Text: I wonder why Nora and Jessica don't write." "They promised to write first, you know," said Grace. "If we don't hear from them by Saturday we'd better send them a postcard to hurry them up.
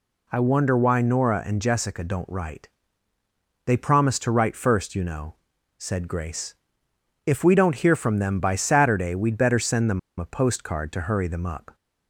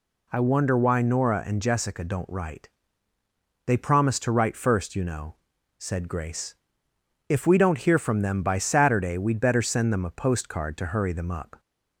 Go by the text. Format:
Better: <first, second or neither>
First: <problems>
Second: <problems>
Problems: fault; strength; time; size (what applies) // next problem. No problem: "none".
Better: second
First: pauses between "them" and "a"; slight; at 9.9 s; 0.19 s long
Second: none